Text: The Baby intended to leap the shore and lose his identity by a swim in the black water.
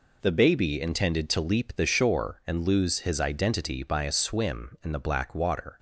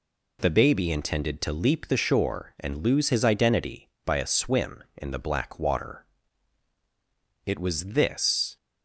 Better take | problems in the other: first | goes on to say "It was this"; noticeable; from 7.4 s on; 1.1 s long

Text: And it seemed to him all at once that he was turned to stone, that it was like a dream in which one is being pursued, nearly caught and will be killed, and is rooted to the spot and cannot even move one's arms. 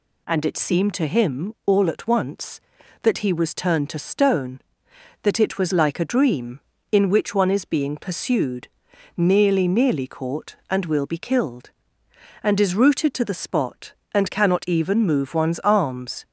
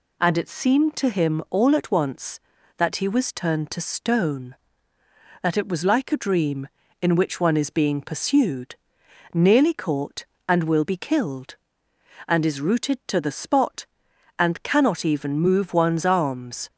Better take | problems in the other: second | says "nearly" twice; at 9.6 s

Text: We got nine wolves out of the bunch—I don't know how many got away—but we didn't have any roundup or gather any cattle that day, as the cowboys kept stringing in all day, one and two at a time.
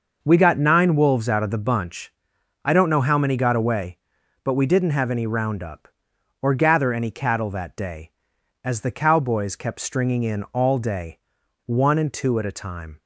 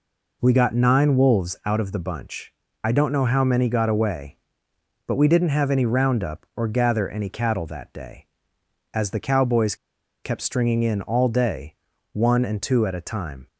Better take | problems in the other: first | pauses between "cowboys" and "kept"; noticeable; at 9.7 s; 0.49 s long

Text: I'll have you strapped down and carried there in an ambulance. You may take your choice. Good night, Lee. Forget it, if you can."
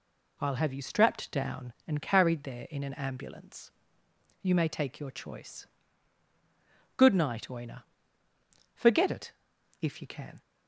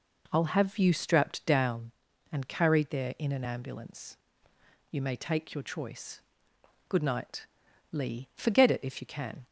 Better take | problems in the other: second | says "Oina" for "Lee"; at 7.4 s

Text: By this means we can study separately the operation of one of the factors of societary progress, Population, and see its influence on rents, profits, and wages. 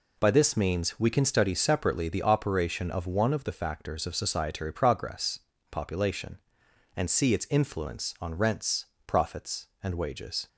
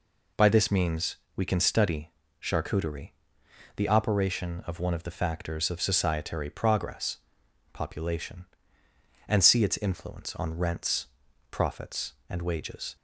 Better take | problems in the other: first | pauses between "means" and "we"; slight; at 1.1 s; 0.18 s long // says "charcuterie" for "separately"; at 2.4 s

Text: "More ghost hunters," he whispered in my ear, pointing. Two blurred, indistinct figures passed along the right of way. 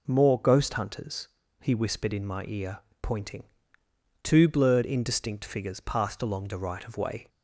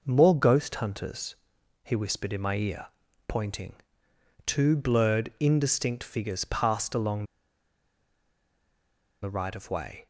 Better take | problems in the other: first | pauses between "along" and "the"; strong; at 7.2 s; 1.9 s long

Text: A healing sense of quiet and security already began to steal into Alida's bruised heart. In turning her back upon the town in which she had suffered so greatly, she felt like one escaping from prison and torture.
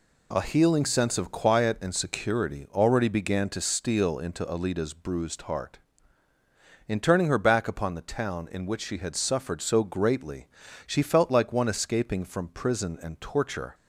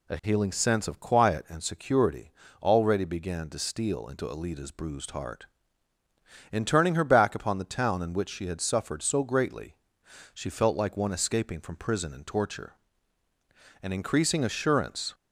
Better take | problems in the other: first | pauses between "security" and "already"; slight; at 2.3 s; 0.32 s long // goes on to say "An increasing assurance"; noticeable; from 13.8 s on; 1.3 s long

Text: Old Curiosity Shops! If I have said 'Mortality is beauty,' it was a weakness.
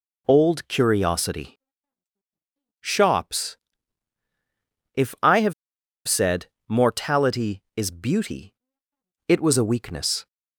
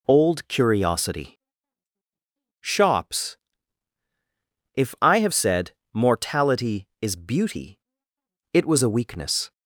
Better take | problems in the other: second | pauses between "Curiosity" and "Shops"; at 1.5 s; 1.2 s long; also in the second // pauses between "have" and "said"; noticeable; at 5.5 s; 0.53 s long // pauses between "said" and "Mortality"; slight; at 6.4 s; 0.20 s long; slight in the second

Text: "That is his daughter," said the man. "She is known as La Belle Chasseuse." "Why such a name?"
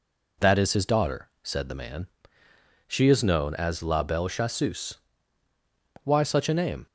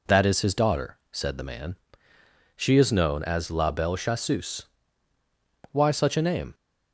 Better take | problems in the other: neither | none

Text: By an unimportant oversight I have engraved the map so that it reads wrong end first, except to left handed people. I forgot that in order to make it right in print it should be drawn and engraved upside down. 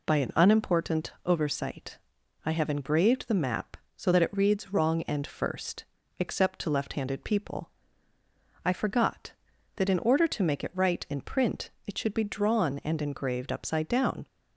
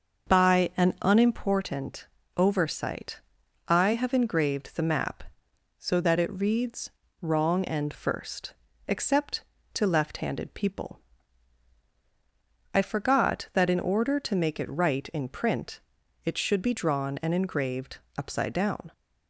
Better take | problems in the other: first | starts louder than the rest; until 1.5 s; 6.5 dB // pauses between "unimportant" and "oversight"; slight; at 2.0 s; 0.30 s long // pauses between "oversight" and "I"; noticeable; at 3.1 s; 0.46 s long; also in the first // pauses between "reads" and "wrong"; slight; at 6.9 s; 0.32 s long // pauses between "print" and "it"; noticeable; at 15.7 s; 0.46 s long; slight in the first // pauses between "engraved" and "upside"; slight; at 17.9 s; 0.20 s long

